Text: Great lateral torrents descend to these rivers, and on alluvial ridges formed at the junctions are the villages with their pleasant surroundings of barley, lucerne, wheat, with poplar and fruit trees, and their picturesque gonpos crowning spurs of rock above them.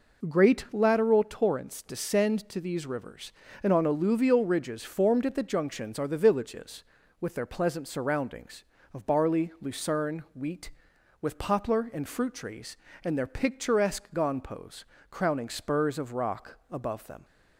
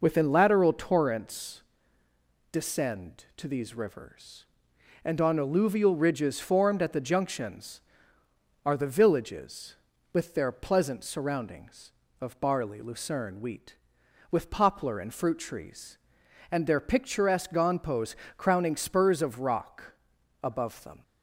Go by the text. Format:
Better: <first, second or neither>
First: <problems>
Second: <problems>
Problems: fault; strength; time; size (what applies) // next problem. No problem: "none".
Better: first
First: pauses between "gonpos" and "crowning"; slight; at 14.8 s; 0.24 s long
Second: says "Within" for "Great"; at 0.0 s // pauses between "torrents" and "descend"; noticeable; at 1.6 s; 0.88 s long // pauses between "gonpos" and "crowning"; slight; at 18.1 s; 0.20 s long // pauses between "rock" and "above"; noticeable; at 19.9 s; 0.50 s long